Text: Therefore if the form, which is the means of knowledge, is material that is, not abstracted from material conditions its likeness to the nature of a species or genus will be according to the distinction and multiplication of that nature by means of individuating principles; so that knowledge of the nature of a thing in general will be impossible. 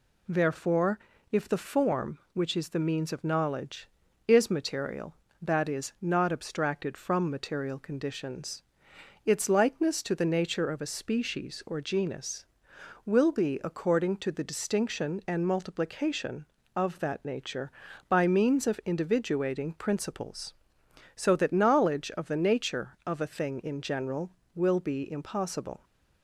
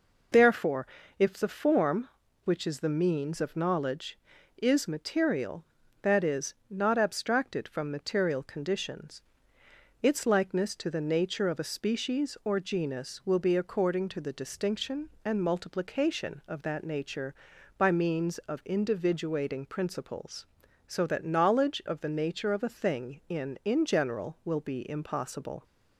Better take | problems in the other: first | pauses between "Therefore" and "if"; slight; at 0.8 s; 0.32 s long; slight in the first // pauses between "conditions" and "its"; noticeable; at 9.2 s; 0.80 s long; noticeable in the first // says "in" twice; at 23.6 s

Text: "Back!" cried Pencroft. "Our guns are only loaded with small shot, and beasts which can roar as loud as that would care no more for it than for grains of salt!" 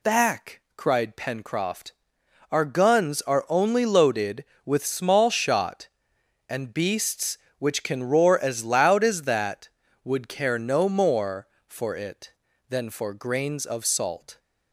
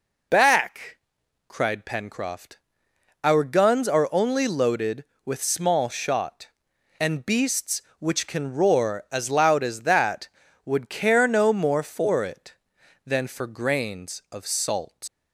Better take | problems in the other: first | leaves "salt" unfinished; at 15.0 s; 115 ms

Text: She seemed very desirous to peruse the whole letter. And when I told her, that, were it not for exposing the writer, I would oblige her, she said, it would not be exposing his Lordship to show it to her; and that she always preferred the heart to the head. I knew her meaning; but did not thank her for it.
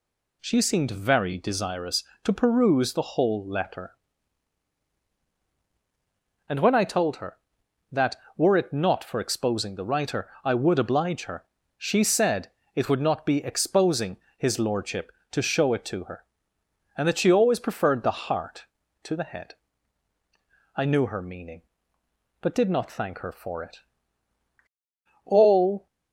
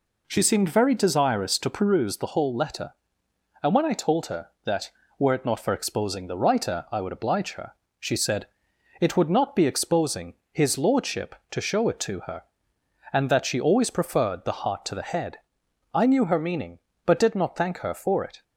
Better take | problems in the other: second | pauses between "exposing" and "his"; slight; at 14.1 s; 0.22 s long; slight in the second // goes on to say "All"; from 25.2 s on; 0.60 s long

